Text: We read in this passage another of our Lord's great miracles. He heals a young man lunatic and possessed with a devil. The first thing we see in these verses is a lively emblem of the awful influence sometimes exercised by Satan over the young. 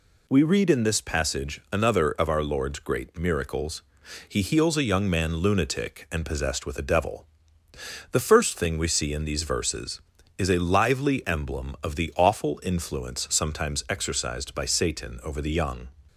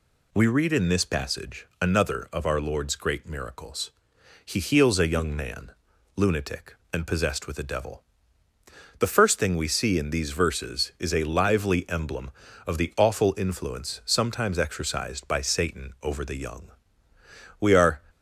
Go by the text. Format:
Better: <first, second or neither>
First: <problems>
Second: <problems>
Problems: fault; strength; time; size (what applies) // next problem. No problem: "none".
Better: first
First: none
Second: pauses between "man" and "lunatic"; at 5.7 s; 0.42 s long // goes on to say "We are"; slight; from 17.5 s on; 0.42 s long